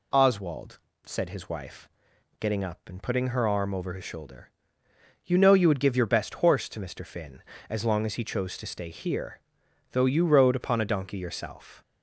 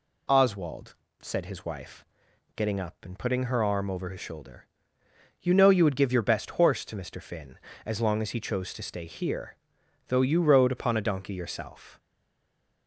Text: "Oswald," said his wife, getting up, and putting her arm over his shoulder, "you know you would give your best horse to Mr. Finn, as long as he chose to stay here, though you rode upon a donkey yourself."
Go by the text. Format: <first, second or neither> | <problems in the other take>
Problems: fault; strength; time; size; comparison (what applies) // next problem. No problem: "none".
first | stays silent after the last word; slight; from 11.9 s on; 0.9 s long